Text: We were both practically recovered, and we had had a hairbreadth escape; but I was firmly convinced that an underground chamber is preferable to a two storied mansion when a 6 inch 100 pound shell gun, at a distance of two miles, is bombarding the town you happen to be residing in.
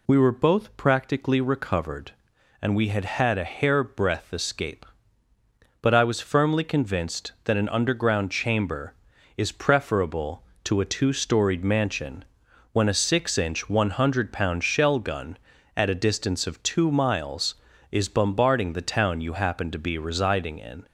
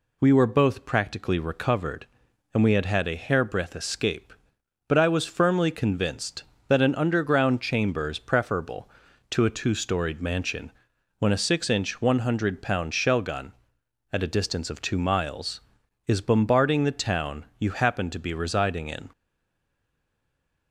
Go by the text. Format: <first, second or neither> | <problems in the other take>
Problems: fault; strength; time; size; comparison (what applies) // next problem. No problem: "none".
first | pauses between "mansion" and "when"; noticeable; at 10.7 s; 0.48 s long; noticeable in the first // stays silent after the last word; noticeable; from 19.1 s on; 1.6 s long